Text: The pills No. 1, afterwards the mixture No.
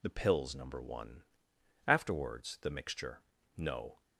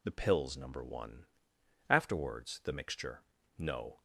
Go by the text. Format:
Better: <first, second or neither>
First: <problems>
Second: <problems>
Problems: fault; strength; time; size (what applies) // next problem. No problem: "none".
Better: neither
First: pauses between "mixture" and "No"; slight; at 3.2 s; 0.34 s long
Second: pauses between "mixture" and "No"; slight; at 3.2 s; 0.34 s long